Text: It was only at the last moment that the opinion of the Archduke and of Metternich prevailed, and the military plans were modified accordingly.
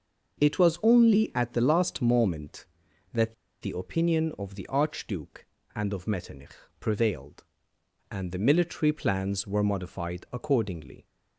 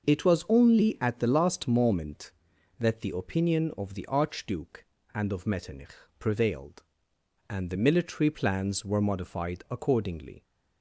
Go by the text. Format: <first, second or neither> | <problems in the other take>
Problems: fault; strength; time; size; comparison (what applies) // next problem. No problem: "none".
second | starts louder than the rest; until 1.4 s; 6 dB; noticeable in the second // pauses between "that" and "the"; slight; at 3.3 s; 0.27 s long // pauses between "Metternich" and "prevailed"; slight; at 6.5 s; 0.24 s long; slight in the second